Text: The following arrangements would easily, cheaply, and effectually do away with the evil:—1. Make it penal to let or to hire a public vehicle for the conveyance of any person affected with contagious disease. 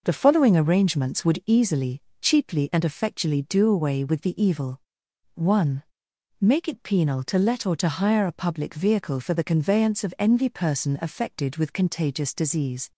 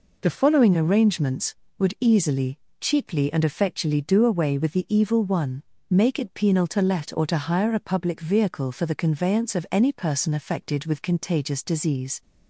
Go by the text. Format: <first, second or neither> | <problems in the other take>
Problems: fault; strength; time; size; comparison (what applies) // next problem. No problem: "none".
second | says "envy" for "any"; at 10.1 s